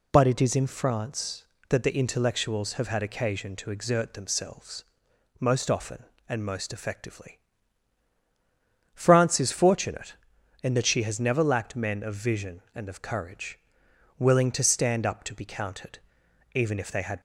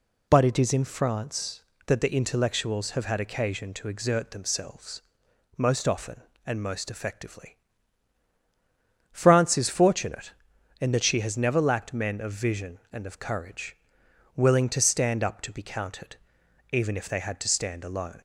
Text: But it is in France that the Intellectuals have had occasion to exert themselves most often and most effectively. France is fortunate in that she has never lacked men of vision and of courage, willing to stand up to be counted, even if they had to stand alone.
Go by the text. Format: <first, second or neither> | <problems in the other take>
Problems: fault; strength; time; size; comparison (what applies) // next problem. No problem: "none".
second | pauses between "themselves" and "most"; noticeable; at 4.8 s; 0.56 s long; noticeable in the second // stops before "to stand alone"; at 17.1 s